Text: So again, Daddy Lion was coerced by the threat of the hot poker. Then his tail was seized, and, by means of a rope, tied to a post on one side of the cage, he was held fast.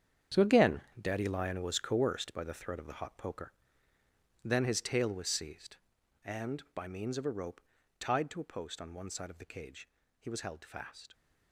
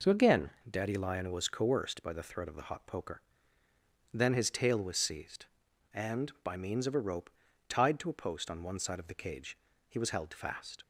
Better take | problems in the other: second | gets quieter; strong; throughout; 12.5 dB

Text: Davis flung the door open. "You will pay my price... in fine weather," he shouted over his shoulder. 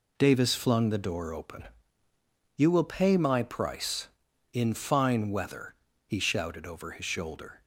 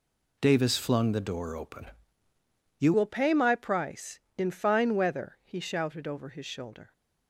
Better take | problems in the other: first | changes voice at "will"; from 2.9 s on; 4.0 s long

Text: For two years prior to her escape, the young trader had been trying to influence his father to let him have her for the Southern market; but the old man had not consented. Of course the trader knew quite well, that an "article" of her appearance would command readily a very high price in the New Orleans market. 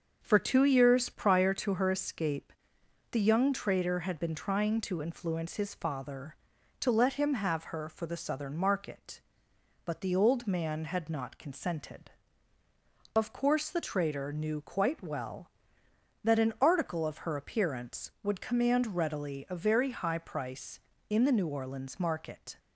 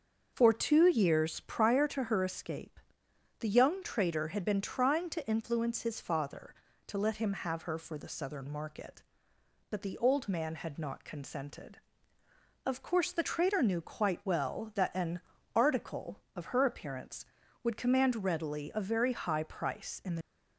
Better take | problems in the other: first | starts louder than the rest; until 1.3 s; 6.5 dB; also in the first // pauses between "an" and "article"; slight; at 15.1 s; 0.34 s long // stops before "New Orleans market"; at 20.2 s

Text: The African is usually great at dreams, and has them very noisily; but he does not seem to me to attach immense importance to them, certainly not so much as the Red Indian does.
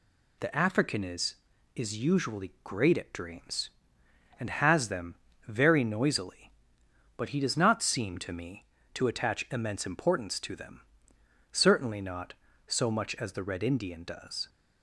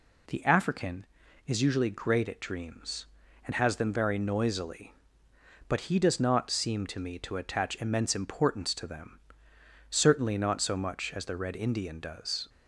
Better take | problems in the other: second | says "is" twice; at 1.7 s // pauses between "them" and "very"; slight; at 5.1 s; 0.32 s long

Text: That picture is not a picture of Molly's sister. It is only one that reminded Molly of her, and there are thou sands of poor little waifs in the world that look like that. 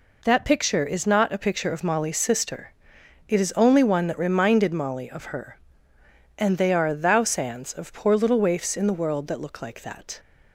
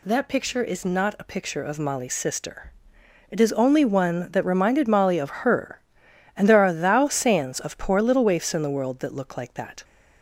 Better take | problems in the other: second | says "they" for "there"; at 6.5 s

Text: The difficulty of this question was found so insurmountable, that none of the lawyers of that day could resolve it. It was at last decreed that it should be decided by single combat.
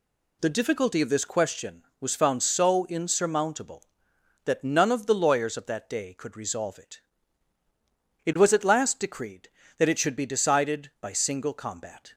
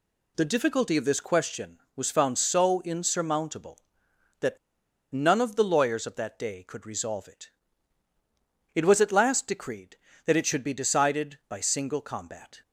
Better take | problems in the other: first | pauses between "that" and "none"; noticeable; at 4.5 s; 0.55 s long

